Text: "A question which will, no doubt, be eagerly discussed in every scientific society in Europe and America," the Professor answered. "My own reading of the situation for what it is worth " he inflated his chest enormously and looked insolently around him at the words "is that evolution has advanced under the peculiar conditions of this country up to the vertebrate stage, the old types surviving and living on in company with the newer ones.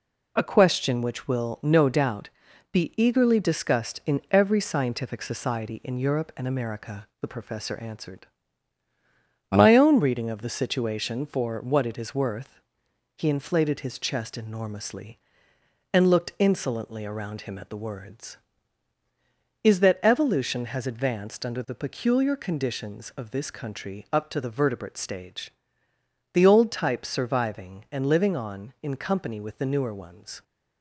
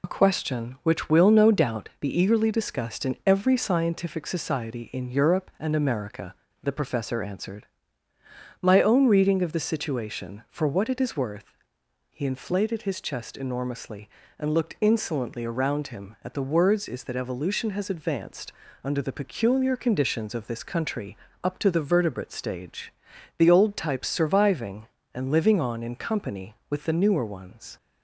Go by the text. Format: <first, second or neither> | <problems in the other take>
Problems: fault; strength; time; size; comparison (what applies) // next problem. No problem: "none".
first | loses the start of "A"; at 0.0 s; 35 ms // pauses between "advanced" and "under"; slight; at 18.5 s; 0.30 s long // pauses between "country" and "up"; slight; at 21.1 s; 0.30 s long